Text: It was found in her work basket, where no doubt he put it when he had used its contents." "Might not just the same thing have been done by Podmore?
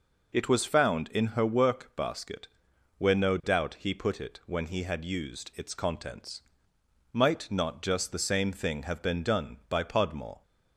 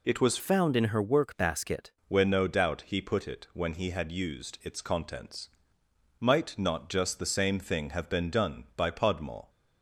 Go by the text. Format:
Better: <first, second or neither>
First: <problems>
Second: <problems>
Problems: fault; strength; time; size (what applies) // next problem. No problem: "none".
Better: first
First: none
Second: changes voice from "found" to "basket"; from 0.3 to 1.9 s; 1.6 s long